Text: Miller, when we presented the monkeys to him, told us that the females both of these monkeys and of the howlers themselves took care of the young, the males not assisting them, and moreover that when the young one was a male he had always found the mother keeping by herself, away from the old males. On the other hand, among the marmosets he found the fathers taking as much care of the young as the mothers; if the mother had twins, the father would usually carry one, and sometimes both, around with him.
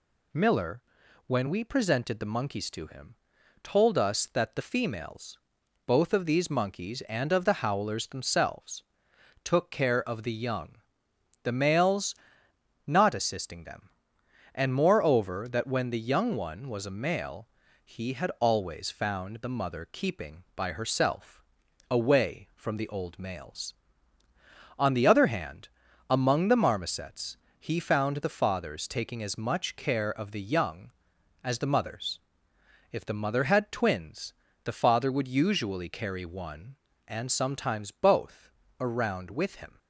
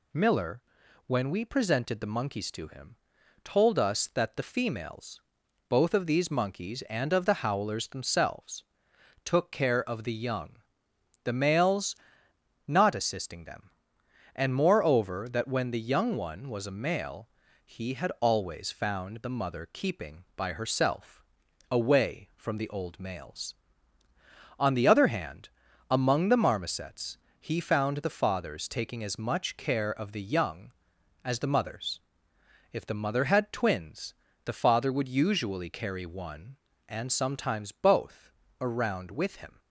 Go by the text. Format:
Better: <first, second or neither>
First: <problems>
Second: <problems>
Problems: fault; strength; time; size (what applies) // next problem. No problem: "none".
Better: neither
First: pauses between "females" and "both"; noticeable; at 5.3 s; 0.48 s long // pauses between "themselves" and "took"; noticeable; at 8.8 s; 0.62 s long // pauses between "males" and "not"; noticeable; at 12.1 s; 0.72 s long // pauses between "male" and "he"; at 17.4 s; 0.38 s long // pauses between "marmosets" and "he"; slight; at 27.3 s; 0.24 s long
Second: pauses between "females" and "both"; noticeable; at 5.2 s; 0.48 s long // pauses between "themselves" and "took"; noticeable; at 8.6 s; 0.62 s long // pauses between "males" and "not"; noticeable; at 11.9 s; 0.72 s long // pauses between "male" and "he"; at 17.2 s; 0.38 s long // pauses between "marmosets" and "he"; slight; at 27.1 s; 0.24 s long